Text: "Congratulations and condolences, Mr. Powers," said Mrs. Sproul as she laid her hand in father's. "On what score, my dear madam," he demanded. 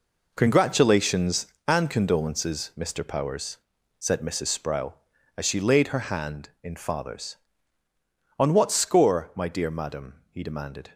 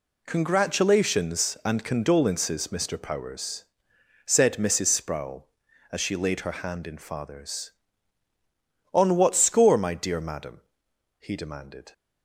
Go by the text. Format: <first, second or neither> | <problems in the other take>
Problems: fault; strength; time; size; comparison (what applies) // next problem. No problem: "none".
second | gets quieter; strong; throughout; 11 dB